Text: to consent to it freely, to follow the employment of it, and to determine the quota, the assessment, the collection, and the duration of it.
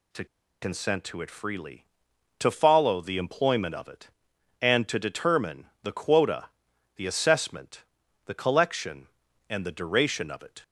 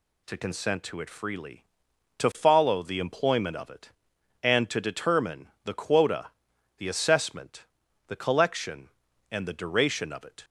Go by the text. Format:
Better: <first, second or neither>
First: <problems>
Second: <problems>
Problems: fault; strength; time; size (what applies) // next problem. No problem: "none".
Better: second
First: pauses between "to" and "consent"; at 0.2 s; 0.36 s long // pauses between "determine" and "the"; slight; at 5.6 s; 0.16 s long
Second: pauses between "determine" and "the"; slight; at 5.4 s; 0.16 s long